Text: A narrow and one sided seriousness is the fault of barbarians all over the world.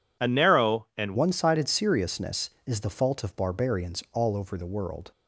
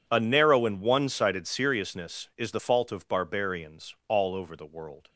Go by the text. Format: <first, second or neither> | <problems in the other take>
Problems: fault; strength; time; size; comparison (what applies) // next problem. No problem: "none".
second | changes voice at "one"; from 1.1 s on; 4.0 s long